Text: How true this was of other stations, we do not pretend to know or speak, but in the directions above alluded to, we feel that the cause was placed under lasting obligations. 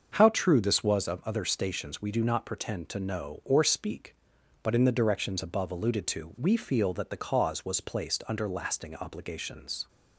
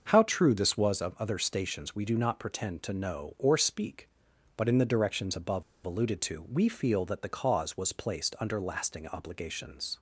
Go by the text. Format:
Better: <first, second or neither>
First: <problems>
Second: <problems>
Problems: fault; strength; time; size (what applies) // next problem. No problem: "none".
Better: first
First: starts louder than the rest; until 1.1 s; 6.5 dB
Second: starts louder than the rest; until 1.1 s; 6.5 dB // pauses between "above" and "alluded"; slight; at 5.6 s; 0.22 s long